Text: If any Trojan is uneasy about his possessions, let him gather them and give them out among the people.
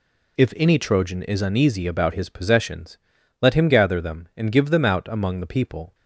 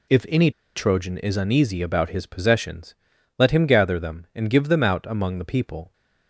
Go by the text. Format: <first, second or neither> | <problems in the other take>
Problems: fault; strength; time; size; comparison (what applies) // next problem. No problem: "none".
first | pauses between "any" and "Trojan"; slight; at 0.4 s; 0.25 s long